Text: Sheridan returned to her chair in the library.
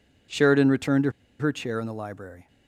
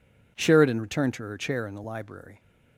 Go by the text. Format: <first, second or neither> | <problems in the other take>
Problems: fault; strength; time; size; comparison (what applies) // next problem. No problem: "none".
second | pauses between "to" and "her"; slight; at 1.1 s; 0.28 s long